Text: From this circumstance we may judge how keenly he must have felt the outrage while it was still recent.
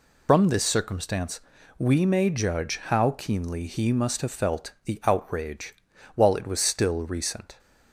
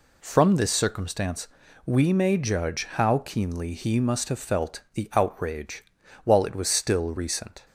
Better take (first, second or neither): second